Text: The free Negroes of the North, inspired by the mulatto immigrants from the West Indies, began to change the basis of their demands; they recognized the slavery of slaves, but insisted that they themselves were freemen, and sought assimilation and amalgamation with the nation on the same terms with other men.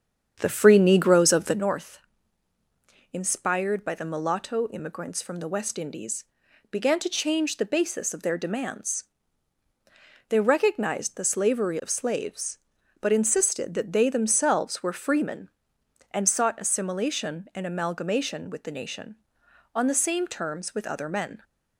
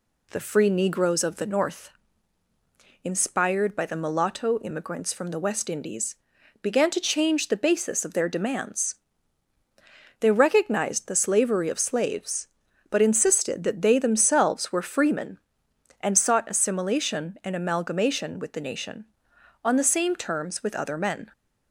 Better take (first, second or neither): second